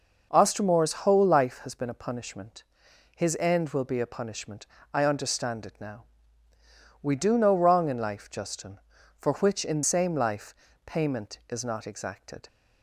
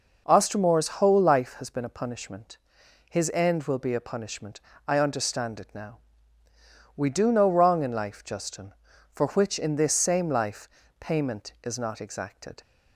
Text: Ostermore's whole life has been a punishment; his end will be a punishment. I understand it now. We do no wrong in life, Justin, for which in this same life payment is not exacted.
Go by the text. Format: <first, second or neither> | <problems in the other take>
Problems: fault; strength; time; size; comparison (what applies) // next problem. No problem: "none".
second | starts louder than the rest; until 1.4 s; 6.5 dB; noticeable in the second // skips "this"; at 9.8 s // pauses between "life" and "payment"; slight; at 10.5 s; 0.30 s long; slight in the second